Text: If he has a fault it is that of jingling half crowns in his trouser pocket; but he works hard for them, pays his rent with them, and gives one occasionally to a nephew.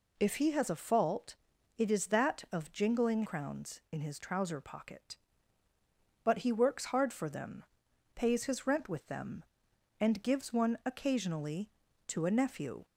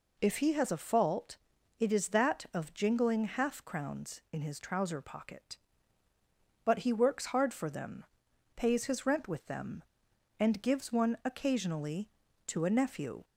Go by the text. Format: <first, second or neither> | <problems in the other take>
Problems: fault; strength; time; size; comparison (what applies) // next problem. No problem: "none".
second | pauses between "fault" and "it"; at 1.3 s; 0.42 s long; also in the second // skips "half"; at 3.2 s